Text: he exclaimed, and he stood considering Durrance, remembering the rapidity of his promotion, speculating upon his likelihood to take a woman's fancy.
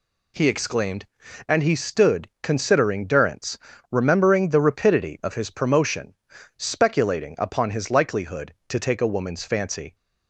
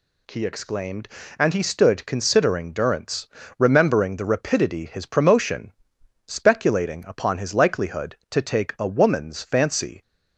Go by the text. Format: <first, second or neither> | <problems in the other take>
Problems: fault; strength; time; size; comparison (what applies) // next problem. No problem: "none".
first | skips "of"; at 4.8 s